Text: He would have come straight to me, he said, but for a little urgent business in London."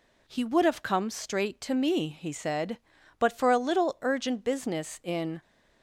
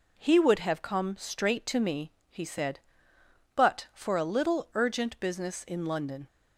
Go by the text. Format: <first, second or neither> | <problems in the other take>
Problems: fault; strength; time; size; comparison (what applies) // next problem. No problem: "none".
second | stops before "London"; at 5.4 s